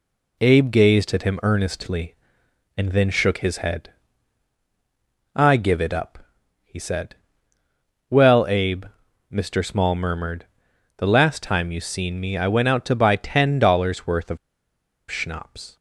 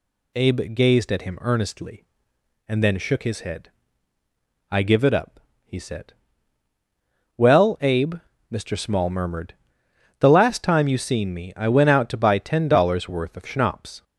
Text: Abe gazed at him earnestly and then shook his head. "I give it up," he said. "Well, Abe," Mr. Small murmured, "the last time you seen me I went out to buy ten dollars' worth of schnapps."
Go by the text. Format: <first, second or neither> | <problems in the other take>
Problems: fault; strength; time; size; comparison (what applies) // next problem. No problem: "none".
second | pauses between "of" and "schnapps"; noticeable; at 14.3 s; 0.72 s long